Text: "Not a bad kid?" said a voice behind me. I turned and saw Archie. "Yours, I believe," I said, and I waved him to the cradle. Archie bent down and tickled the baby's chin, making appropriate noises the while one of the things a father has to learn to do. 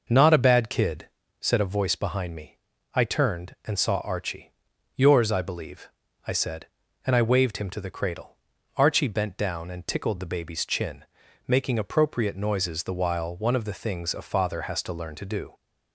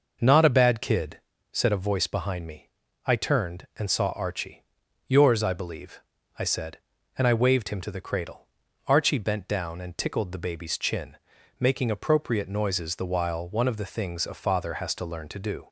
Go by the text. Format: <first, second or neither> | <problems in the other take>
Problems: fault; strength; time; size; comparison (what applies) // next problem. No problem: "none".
neither | none